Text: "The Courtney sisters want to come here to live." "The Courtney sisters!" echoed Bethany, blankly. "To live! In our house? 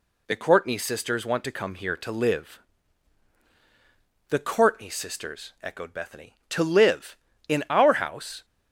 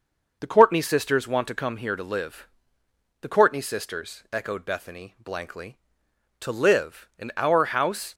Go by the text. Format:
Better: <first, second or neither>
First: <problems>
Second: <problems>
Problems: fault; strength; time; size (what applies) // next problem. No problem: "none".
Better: second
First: skips "blankly"; at 6.4 s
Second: none